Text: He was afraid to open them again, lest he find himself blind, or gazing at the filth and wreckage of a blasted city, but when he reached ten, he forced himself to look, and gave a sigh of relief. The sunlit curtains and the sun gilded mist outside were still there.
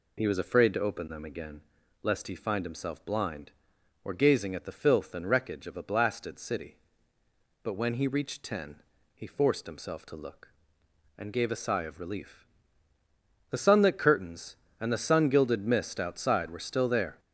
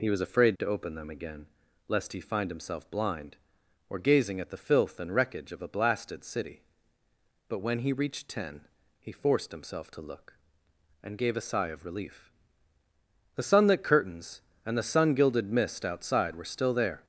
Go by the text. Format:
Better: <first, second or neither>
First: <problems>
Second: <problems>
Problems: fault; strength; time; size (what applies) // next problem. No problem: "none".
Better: neither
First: none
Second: none